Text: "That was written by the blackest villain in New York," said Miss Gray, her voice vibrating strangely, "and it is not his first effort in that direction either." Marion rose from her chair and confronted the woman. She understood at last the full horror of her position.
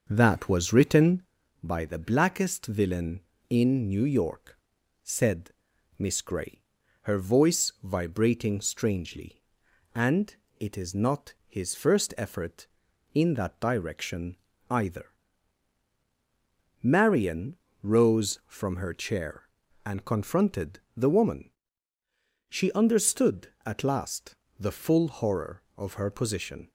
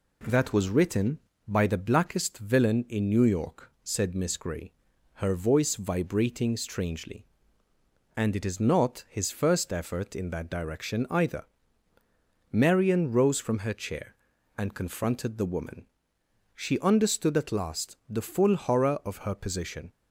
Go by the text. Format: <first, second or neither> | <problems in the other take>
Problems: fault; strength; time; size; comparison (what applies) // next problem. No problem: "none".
second | starts louder than the rest; noticeable; until 1.4 s; 6 dB // pauses between "said" and "Miss"; noticeable; at 5.4 s; 0.48 s long // pauses between "and" and "it"; slight; at 10.3 s; 0.22 s long // pauses between "direction" and "either"; slight; at 14.3 s; 0.34 s long // pauses between "Marion" and "rose"; slight; at 17.5 s; 0.26 s long // pauses between "confronted" and "the"; slight; at 20.7 s; 0.18 s long // pauses between "last" and "the"; slight; at 24.3 s; 0.24 s long